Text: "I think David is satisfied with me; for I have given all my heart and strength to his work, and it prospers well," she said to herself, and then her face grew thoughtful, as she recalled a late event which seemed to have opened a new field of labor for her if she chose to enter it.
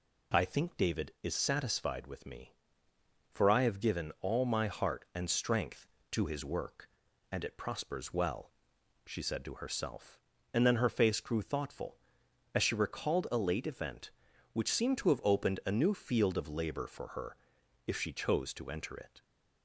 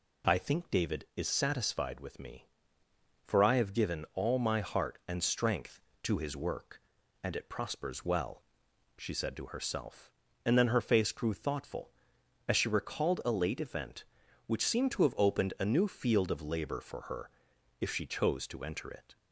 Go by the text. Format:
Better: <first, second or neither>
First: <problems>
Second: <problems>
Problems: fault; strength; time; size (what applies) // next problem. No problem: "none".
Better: neither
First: pauses between "her" and "if"; noticeable; at 17.3 s; 0.52 s long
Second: pauses between "her" and "if"; noticeable; at 17.2 s; 0.52 s long